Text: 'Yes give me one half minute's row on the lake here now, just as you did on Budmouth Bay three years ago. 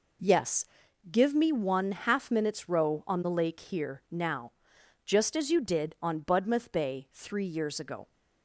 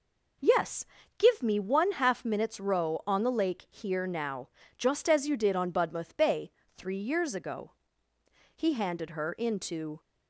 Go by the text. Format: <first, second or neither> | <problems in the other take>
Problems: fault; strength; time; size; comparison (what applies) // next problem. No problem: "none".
first | pauses between "Yes" and "give"; slight; at 0.8 s; 0.34 s long; also in the first // pauses between "Bay" and "three"; slight; at 6.5 s; 0.23 s long // goes on to say "He handed her into"; from 8.5 s on; 1.4 s long